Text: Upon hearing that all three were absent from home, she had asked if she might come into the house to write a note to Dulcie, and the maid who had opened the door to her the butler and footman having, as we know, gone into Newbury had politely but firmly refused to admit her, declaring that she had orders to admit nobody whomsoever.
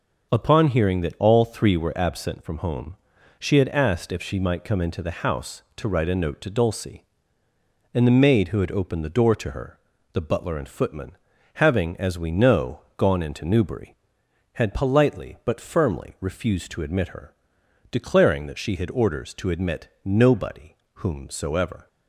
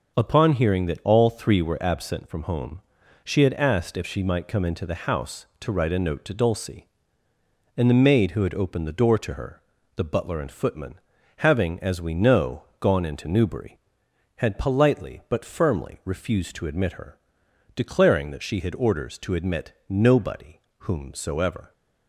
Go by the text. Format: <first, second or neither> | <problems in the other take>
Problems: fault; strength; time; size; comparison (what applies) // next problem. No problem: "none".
neither | pauses between "her" and "the"; slight; the same in both // pauses between "footman" and "having"; the same in both // pauses between "admit" and "nobody"; slight; the same in both // pauses between "nobody" and "whomsoever"; slight; the same in both